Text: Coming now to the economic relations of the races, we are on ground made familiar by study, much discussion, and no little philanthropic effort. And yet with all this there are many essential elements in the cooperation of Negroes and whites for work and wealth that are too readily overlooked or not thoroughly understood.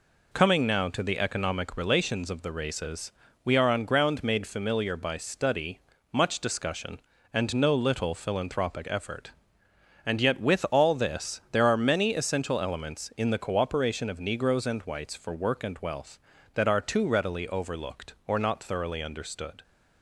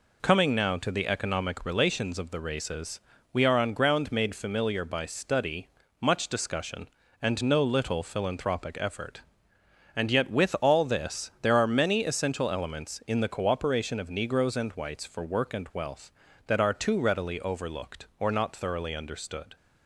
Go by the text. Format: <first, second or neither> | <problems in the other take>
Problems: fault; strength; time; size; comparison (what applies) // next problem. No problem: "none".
neither | none